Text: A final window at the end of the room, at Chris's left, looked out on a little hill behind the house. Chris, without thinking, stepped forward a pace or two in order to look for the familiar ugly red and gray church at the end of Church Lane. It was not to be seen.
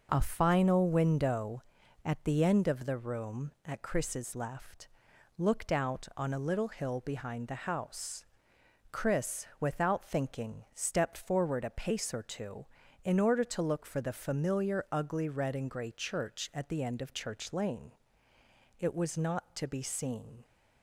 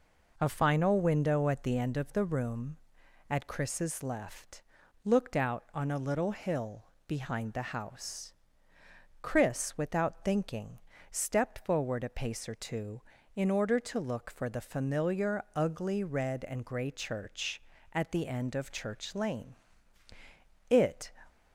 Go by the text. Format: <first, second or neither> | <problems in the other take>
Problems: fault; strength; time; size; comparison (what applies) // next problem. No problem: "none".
first | pauses between "hill" and "behind"; slight; at 6.8 s; 0.22 s long // stops before "was not to be seen"; at 21.2 s